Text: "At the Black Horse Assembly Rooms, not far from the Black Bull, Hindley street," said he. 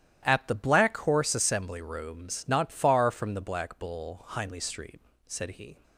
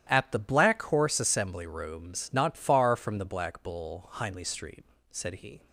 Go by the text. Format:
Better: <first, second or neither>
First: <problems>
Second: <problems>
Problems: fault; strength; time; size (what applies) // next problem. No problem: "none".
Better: neither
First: starts louder than the rest; strong; until 1.3 s; 13 dB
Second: starts louder than the rest; strong; until 1.1 s; 13 dB